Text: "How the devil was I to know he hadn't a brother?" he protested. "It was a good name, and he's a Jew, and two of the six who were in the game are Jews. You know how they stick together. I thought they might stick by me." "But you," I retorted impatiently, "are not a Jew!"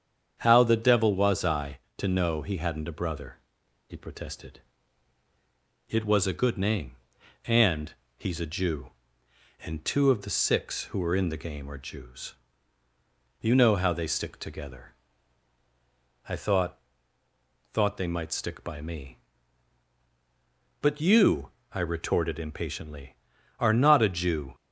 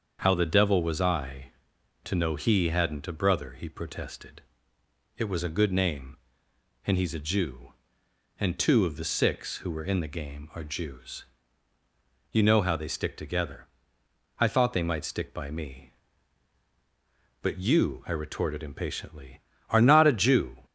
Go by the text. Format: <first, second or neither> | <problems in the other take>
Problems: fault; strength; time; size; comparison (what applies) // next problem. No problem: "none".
second | starts louder than the rest; strong; until 1.4 s; 8 dB; also in the second // pauses between "and" and "he's"; slight; at 7.9 s; 0.24 s long // says "thought" twice; at 17.7 s